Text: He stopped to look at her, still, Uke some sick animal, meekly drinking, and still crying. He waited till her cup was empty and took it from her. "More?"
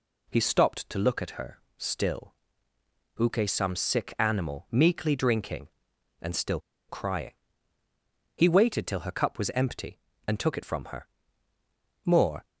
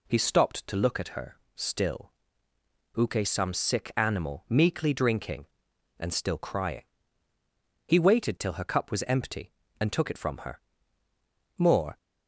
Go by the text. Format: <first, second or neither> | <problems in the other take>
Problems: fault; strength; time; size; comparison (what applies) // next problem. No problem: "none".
second | pauses between "still" and "crying"; slight; at 6.5 s; 0.29 s long